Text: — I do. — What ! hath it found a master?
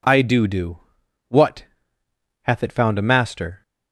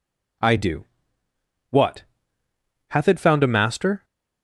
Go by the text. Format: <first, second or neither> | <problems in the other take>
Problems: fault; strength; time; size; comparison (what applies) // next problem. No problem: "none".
second | says "do" twice; at 0.4 s